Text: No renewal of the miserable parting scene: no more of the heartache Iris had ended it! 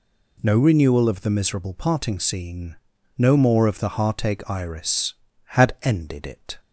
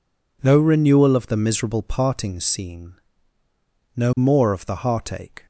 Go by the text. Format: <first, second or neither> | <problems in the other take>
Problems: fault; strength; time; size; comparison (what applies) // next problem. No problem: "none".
first | stops before "Iris had ended it"; at 5.4 s